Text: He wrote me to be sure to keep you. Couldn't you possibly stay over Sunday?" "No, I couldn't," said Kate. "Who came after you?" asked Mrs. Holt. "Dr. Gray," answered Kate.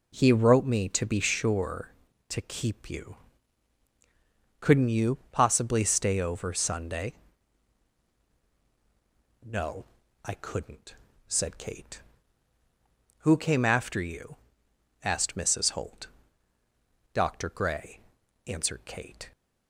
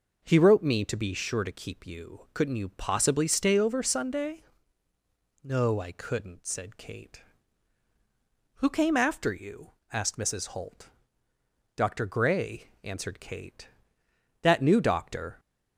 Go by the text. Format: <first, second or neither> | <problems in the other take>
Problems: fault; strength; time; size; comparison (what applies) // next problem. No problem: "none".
first | goes on to say "That new doctor"; noticeable; from 14.4 s on; 0.96 s long